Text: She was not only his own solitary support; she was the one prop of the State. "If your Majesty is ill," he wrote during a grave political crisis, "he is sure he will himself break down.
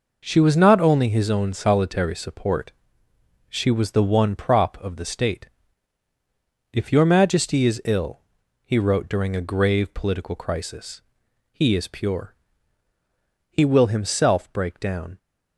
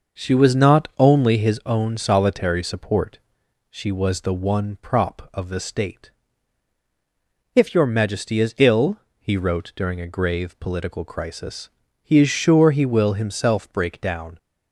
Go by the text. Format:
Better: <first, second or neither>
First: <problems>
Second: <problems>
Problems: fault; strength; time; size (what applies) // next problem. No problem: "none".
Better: second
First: says "pure" for "sure"; at 11.8 s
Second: none